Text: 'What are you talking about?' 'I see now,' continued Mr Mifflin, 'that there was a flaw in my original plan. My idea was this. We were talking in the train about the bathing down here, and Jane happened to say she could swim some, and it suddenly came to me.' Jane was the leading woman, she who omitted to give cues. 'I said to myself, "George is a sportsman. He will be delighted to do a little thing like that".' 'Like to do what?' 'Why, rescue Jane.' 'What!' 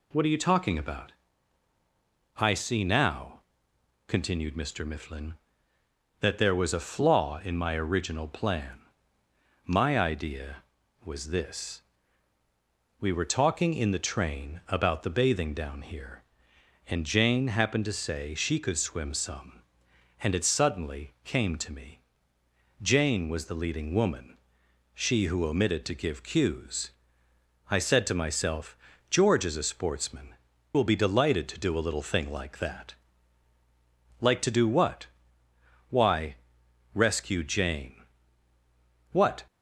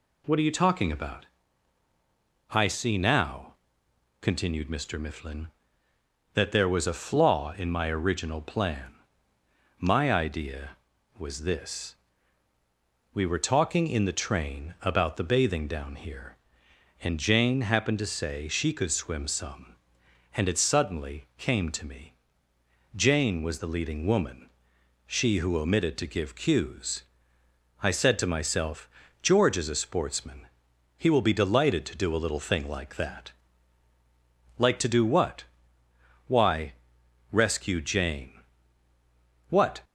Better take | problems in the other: second | skips "He"; at 30.5 s

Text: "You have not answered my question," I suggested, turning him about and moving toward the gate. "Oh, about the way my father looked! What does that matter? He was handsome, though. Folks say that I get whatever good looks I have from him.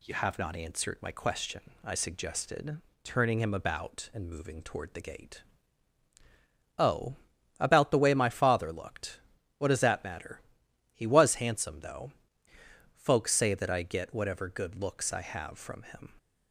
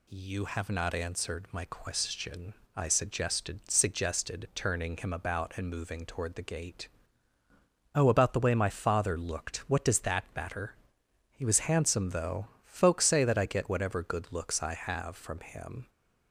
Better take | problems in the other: first | says "suggested" twice; at 3.6 s

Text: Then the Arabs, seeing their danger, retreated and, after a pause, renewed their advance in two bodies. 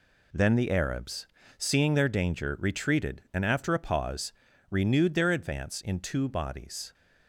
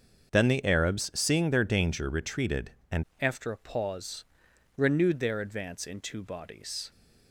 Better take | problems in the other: first | starts louder than the rest; until 1.4 s; 6.5 dB // changes voice at "after"; from 3.1 s on; 3.7 s long

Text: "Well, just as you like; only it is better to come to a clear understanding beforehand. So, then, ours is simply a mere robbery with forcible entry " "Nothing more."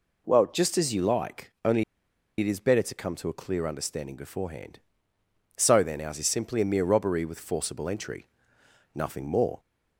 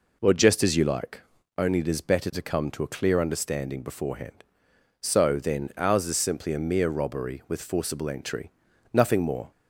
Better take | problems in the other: second | pauses between "only" and "it"; noticeable; at 1.8 s; 0.55 s long

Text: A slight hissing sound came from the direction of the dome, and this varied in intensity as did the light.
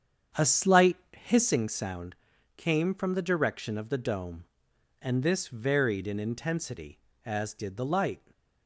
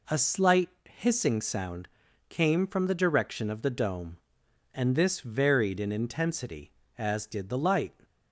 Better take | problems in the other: second | starts louder than the rest; strong; until 1.6 s; 8 dB // pauses between "slight" and "hissing"; slight; at 0.9 s; 0.18 s long; slight in the second // pauses between "sound" and "came"; at 2.1 s; 0.42 s long; also in the second

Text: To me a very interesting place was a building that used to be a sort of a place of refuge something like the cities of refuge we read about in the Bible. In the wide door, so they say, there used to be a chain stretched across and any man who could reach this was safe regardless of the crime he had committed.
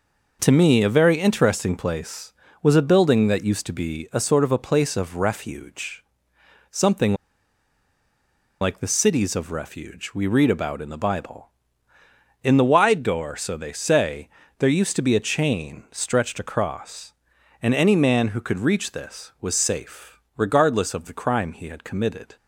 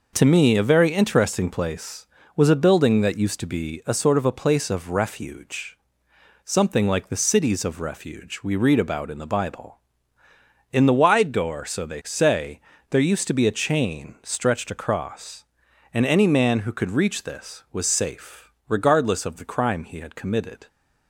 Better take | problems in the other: second | pauses between "refuge" and "something"; noticeable; at 6.0 s; 0.70 s long; noticeable in the second // pauses between "something" and "like"; strong; at 7.1 s; 1.4 s long // pauses between "safe" and "regardless"; slight; at 20.2 s; 0.16 s long; slight in the second

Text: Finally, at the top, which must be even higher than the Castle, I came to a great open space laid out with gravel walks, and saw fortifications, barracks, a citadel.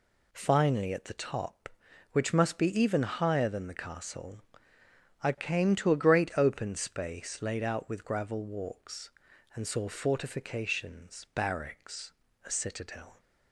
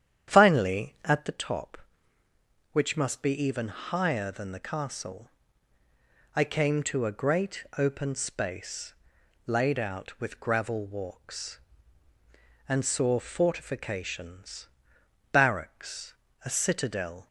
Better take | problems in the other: first | starts louder than the rest; strong; until 1.4 s; 9.5 dB // pauses between "space" and "laid"; noticeable; at 8.9 s; 0.54 s long

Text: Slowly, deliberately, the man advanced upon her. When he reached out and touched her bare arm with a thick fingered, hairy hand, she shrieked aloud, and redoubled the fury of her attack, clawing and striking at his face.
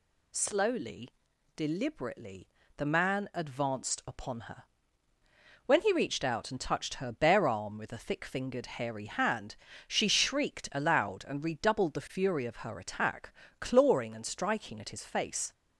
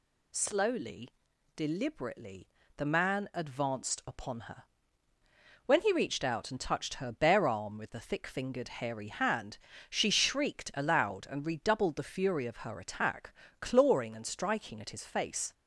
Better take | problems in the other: neither | none

